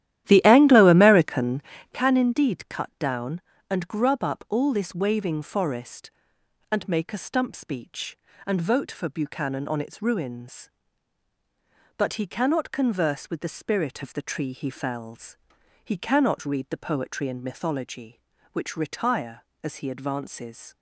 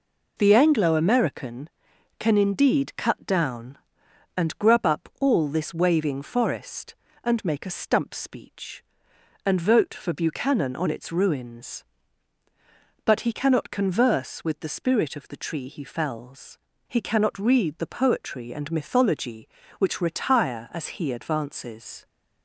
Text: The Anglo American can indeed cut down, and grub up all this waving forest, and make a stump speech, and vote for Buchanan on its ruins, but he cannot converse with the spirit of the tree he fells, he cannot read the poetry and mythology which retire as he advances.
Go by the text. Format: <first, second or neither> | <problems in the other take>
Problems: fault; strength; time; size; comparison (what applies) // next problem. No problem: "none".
second | starts louder than the rest; strong; until 2.1 s; 12.5 dB